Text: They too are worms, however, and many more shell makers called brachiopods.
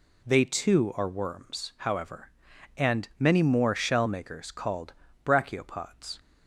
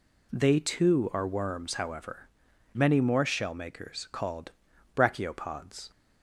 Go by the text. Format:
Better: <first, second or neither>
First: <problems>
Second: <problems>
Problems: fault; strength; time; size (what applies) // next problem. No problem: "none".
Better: first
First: pauses between "called" and "brachiopods"; slight; at 4.9 s; 0.32 s long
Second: skips "and"; at 2.5 s // pauses between "called" and "brachiopods"; at 4.5 s; 0.44 s long